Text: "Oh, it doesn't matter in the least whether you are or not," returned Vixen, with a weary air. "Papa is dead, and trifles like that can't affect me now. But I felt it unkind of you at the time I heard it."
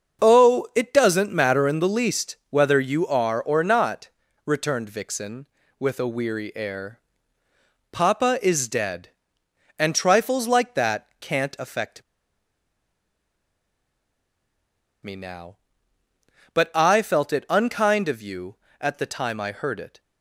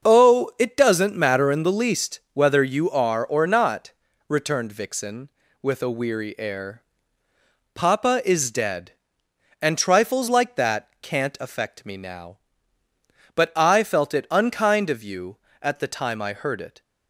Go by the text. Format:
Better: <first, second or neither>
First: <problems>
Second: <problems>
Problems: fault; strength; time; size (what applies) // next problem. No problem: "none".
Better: second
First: starts louder than the rest; until 1.2 s; 6.5 dB // pauses between "affect" and "me"; strong; at 12.0 s; 3.0 s long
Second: starts louder than the rest; until 1.1 s; 6.5 dB